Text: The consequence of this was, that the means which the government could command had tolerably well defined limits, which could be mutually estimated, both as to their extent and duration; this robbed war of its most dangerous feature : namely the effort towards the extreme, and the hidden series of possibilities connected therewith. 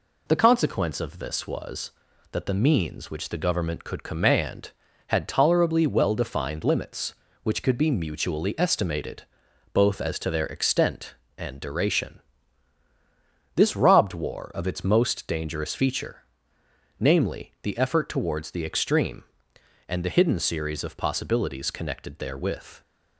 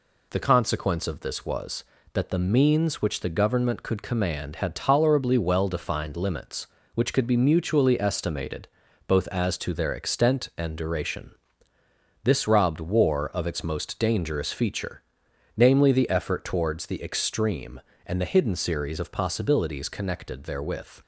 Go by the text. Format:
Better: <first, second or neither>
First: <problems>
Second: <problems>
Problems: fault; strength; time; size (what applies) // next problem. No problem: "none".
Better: neither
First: none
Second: none